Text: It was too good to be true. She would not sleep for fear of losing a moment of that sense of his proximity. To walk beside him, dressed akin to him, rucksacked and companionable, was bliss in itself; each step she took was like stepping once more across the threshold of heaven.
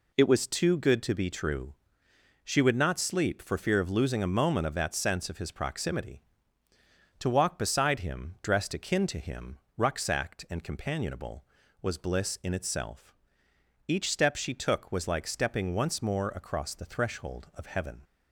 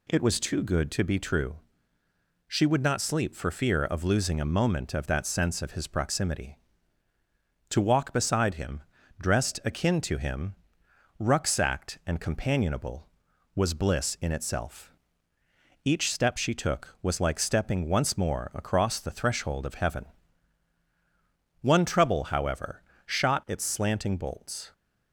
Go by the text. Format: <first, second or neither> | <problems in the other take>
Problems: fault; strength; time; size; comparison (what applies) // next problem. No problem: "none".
first | goes on to say "One trouble however shot its slanting bolts"; strong; from 21.5 s on; 3.1 s long